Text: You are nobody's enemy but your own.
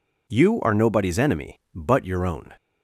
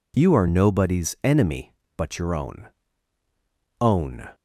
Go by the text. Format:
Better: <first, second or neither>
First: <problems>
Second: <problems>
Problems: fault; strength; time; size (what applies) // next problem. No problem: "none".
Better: first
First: none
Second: says "own" twice; at 3.8 s